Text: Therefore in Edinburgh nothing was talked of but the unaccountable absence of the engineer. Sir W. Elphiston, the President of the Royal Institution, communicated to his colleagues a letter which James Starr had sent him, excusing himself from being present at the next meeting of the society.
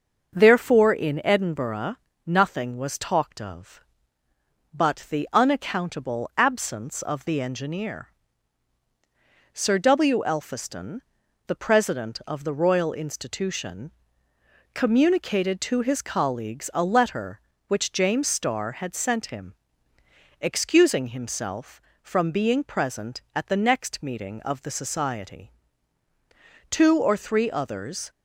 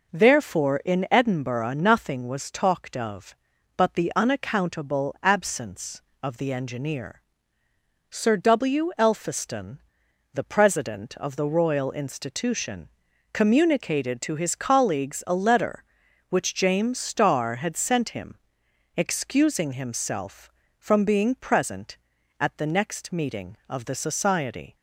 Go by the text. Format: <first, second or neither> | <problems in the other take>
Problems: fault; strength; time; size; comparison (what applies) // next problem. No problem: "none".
second | starts louder than the rest; until 1.3 s; 6.5 dB // pauses between "Edinburgh" and "nothing"; slight; at 1.9 s; 0.30 s long // goes on to say "Two or three others"; from 26.7 s on; 1.3 s long